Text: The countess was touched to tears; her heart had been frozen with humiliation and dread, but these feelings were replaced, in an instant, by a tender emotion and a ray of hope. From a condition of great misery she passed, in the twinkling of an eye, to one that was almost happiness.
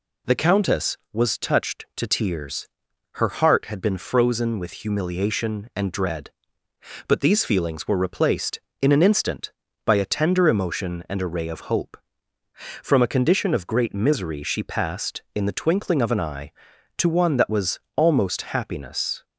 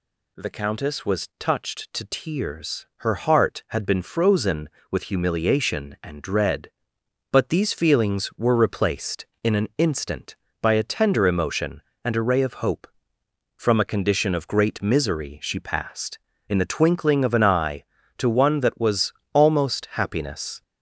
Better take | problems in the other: neither | pauses between "was" and "almost"; slight; the same in both

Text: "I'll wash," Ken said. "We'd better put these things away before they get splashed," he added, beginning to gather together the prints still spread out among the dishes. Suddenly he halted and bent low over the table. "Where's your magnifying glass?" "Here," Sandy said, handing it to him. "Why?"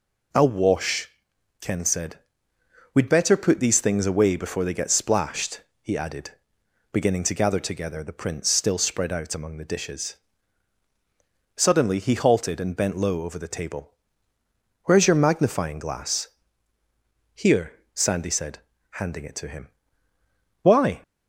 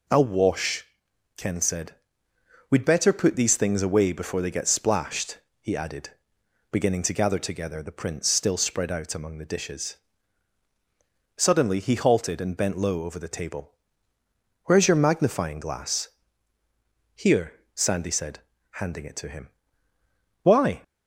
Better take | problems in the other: neither | none

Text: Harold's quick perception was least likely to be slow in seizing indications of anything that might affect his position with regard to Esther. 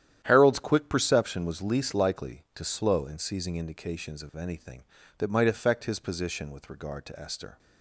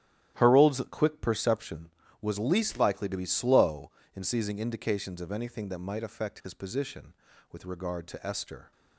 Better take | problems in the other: second | starts louder than the rest; strong; until 1.2 s; 10.5 dB; strong in the second // skips "be"; at 2.6 s

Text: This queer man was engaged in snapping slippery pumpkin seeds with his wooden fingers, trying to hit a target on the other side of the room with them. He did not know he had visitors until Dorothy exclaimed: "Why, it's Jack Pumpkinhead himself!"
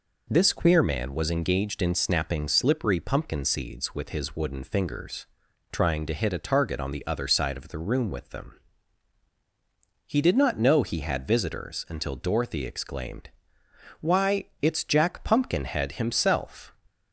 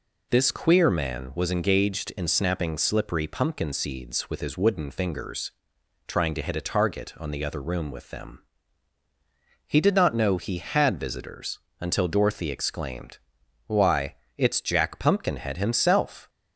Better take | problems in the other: first | skips "side of the"; at 7.6 s // pauses between "visitors" and "until"; slight; at 11.5 s; 0.20 s long

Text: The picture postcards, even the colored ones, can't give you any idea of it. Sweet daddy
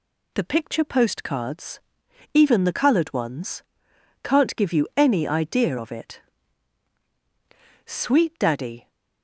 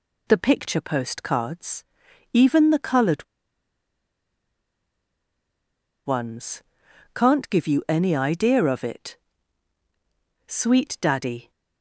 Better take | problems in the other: first | pauses between "colored" and "ones"; strong; at 3.2 s; 2.8 s long

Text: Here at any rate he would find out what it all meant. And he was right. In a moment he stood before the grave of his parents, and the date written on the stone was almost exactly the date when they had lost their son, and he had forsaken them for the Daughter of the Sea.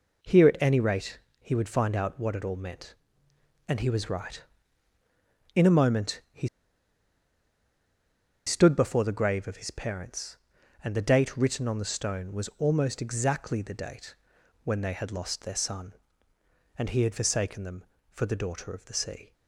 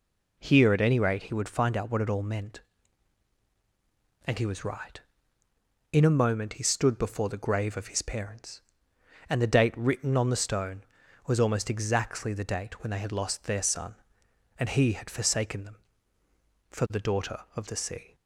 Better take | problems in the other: second | pauses between "rate" and "he"; slight; at 1.1 s; 0.20 s long // pauses between "he" and "stood"; strong; at 6.4 s; 1.9 s long // pauses between "date" and "when"; noticeable; at 14.1 s; 0.48 s long

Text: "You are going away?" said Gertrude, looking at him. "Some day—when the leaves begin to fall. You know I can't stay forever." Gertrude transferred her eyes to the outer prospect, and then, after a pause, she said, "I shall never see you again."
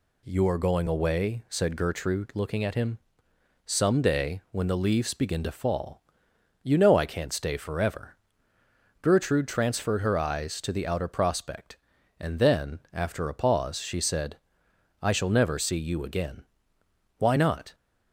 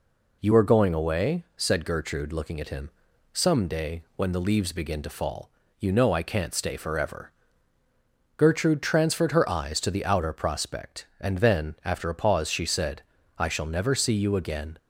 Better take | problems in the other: second | goes on to say "Why not"; from 17.1 s on; 0.57 s long

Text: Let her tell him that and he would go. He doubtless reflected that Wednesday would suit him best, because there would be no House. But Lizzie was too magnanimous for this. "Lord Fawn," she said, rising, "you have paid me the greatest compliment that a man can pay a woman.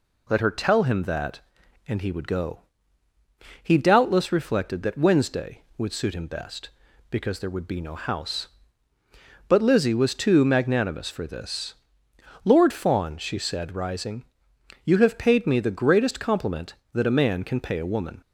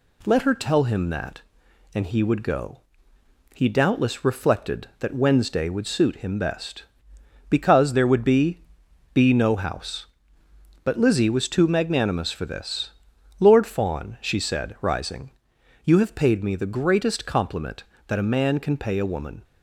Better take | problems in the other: first | says "be" twice; at 9.1 s

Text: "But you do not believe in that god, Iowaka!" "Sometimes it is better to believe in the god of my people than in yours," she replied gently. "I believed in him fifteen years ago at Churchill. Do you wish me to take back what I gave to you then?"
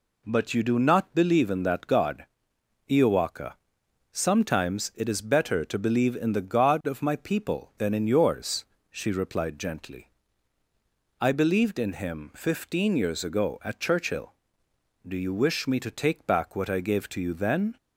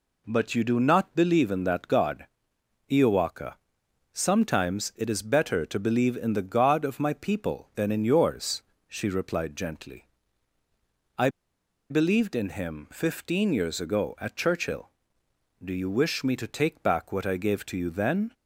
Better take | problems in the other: first | pauses between "I" and "believed"; noticeable; at 11.2 s; 0.62 s long

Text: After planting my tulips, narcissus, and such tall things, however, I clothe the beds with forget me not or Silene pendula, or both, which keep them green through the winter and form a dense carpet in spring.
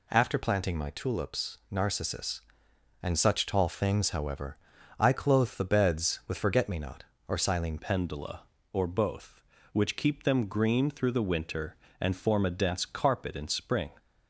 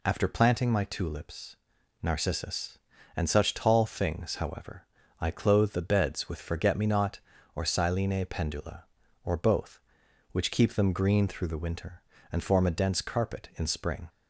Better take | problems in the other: second | changes voice at "pendula"; from 7.7 s on; 6.2 s long

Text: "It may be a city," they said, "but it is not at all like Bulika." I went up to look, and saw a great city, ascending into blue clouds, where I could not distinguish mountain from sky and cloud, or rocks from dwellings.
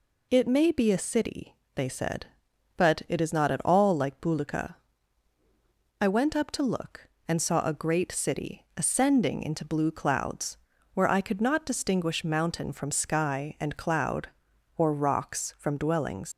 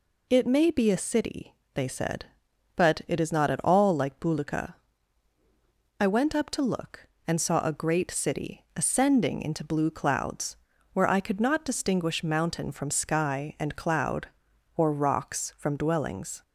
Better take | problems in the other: second | leaves "dwellings" unfinished; at 16.3 s; 110 ms

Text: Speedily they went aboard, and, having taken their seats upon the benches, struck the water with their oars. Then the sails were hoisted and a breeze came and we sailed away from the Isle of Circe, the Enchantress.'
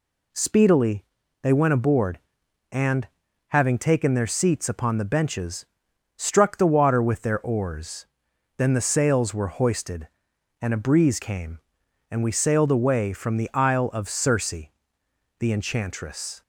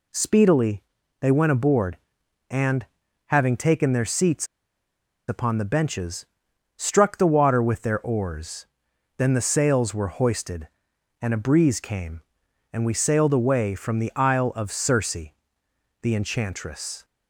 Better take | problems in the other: first | pauses between "Speedily" and "they"; at 0.8 s; 0.38 s long; also in the first // pauses between "seats" and "upon"; noticeable; at 4.4 s; 0.82 s long

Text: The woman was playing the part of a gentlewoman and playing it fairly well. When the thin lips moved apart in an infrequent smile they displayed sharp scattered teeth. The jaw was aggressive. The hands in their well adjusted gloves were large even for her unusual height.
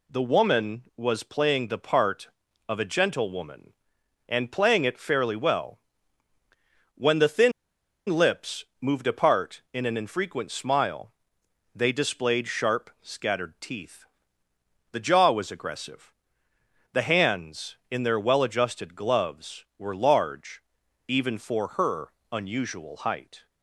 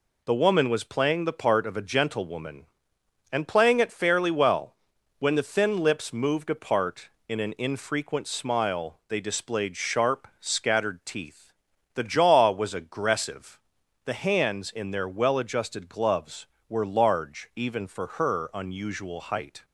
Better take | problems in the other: second | pauses between "thin" and "lips"; noticeable; at 7.5 s; 0.57 s long // pauses between "smile" and "they"; noticeable; at 11.1 s; 0.62 s long // pauses between "large" and "even"; noticeable; at 20.6 s; 0.46 s long // pauses between "her" and "unusual"; slight; at 22.1 s; 0.20 s long

